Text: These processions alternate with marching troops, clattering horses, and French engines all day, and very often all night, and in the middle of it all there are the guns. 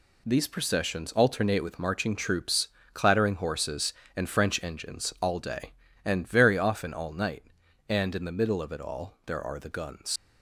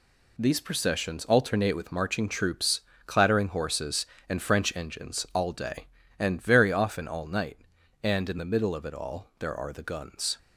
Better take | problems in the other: second | leaves "guns" unfinished; at 10.1 s; 85 ms

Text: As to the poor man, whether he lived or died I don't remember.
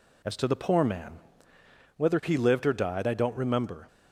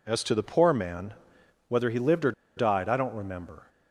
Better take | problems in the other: first | pauses between "or" and "died"; slight; at 2.3 s; 0.24 s long

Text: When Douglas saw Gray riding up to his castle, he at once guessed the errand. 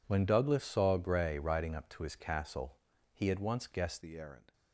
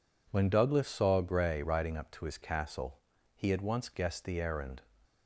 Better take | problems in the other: second | changes voice at "the"; from 4.0 s on; 0.5 s long

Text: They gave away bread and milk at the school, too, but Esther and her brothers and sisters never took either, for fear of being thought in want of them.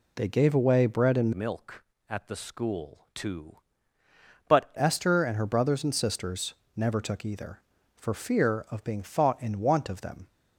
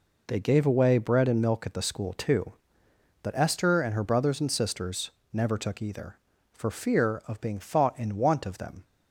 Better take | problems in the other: second | changes voice from "milk" to "but"; from 1.3 to 4.7 s; 3.4 s long // pauses between "sisters" and "never"; slight; at 6.5 s; 0.22 s long; slight in the second

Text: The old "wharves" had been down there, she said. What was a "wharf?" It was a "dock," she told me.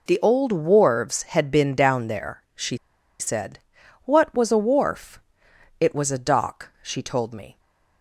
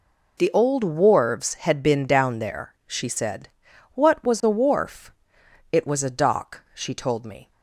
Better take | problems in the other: second | pauses between "she" and "said"; at 2.7 s; 0.42 s long

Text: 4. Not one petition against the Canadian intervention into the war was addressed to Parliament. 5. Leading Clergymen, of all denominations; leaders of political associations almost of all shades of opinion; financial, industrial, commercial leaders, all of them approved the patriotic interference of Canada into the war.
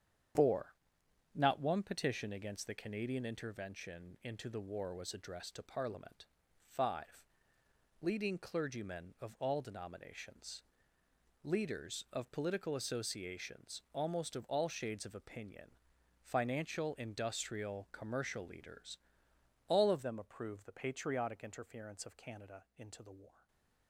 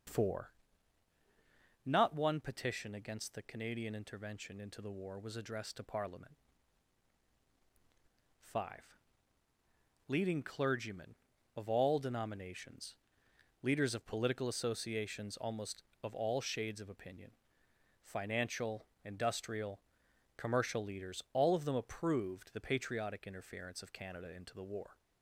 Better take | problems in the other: second | starts louder than the rest; strong; until 1.9 s; 8.5 dB; also in the second // changes voice at "them"; from 20.0 s on; 3.4 s long // stays silent after the last word; slight; from 23.2 s on; 0.6 s long

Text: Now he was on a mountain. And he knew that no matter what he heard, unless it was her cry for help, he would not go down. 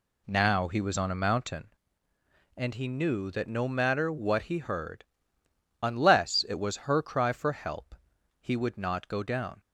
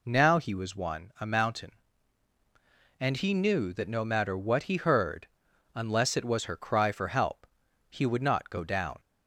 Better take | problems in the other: first | says "one" for "on"; at 0.7 s

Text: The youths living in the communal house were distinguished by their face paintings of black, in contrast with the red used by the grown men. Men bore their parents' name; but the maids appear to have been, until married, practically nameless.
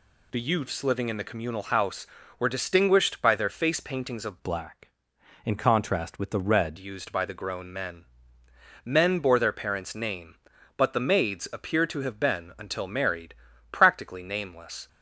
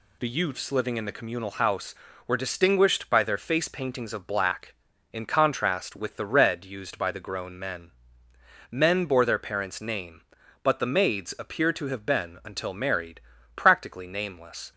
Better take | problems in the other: second | changes voice from "black" to "red"; from 4.4 to 6.7 s; 2.3 s long

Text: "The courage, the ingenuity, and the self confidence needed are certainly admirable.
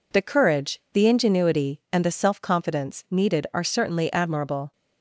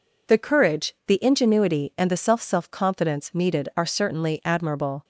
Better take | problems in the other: first | says "self" twice; at 2.3 s

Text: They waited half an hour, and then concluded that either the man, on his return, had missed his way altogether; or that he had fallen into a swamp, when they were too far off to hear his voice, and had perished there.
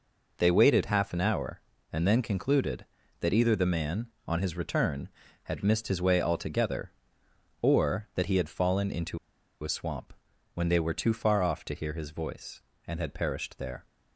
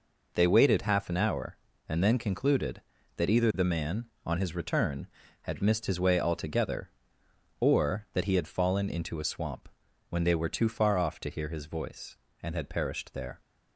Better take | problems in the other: second | pauses between "into" and "a"; at 9.1 s; 0.45 s long

